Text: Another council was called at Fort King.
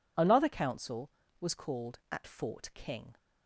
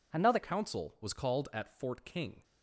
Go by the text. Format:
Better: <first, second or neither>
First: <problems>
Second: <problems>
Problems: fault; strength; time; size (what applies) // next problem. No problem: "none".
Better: first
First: none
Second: changes voice at "council"; from 0.4 s on; 2.0 s long